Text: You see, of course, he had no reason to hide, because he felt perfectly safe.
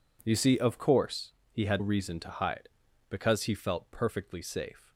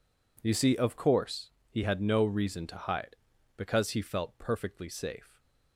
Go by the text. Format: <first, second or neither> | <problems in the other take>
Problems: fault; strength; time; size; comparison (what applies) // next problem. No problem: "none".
second | skips "no"; at 1.7 s